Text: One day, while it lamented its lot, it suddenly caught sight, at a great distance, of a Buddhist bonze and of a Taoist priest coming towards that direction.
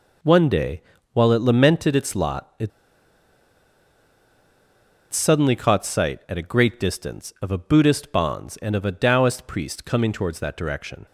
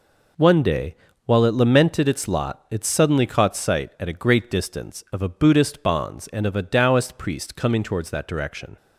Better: second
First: pauses between "it" and "suddenly"; strong; at 2.7 s; 2.4 s long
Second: none

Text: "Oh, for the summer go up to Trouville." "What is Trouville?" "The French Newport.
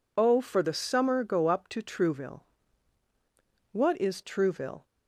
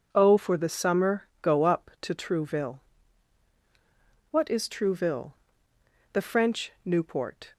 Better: second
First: stops before "The French Newport"; at 4.8 s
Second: none

